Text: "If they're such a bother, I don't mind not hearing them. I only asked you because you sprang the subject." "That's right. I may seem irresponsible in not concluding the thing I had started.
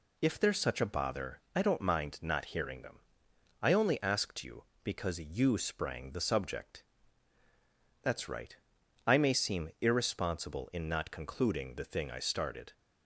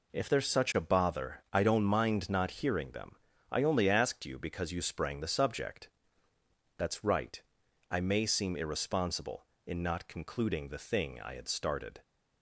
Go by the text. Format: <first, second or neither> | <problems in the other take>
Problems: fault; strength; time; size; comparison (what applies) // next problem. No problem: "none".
second | skips "had"; at 12.1 s